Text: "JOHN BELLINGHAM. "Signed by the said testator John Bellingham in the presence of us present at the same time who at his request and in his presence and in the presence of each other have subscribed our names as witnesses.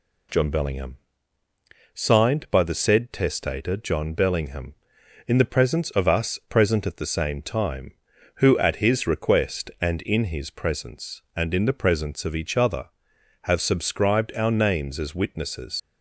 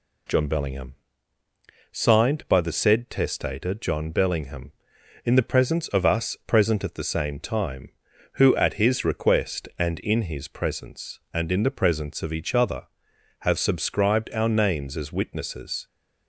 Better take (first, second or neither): second